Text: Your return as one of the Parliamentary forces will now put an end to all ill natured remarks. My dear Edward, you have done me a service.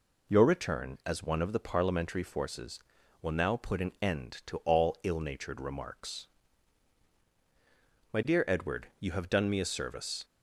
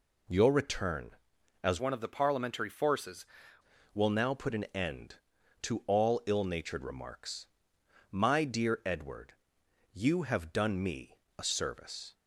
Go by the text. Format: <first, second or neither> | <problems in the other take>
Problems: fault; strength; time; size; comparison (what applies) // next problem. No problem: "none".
first | changes voice from "one" to "forces"; from 1.7 to 3.2 s; 1.5 s long // pauses between "me" and "a"; slight; at 11.1 s; 0.22 s long